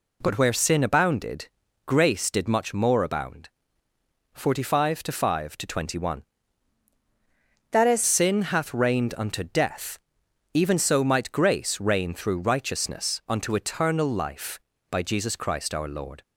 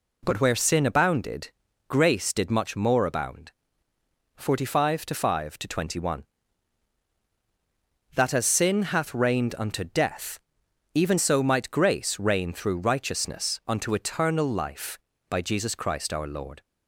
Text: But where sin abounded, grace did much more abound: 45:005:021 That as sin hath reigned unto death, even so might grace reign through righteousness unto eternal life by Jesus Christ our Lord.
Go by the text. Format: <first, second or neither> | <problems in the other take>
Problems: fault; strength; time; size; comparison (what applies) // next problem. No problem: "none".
second | changes voice from "That" to "as"; from 7.7 to 8.0 s; 0.3 s long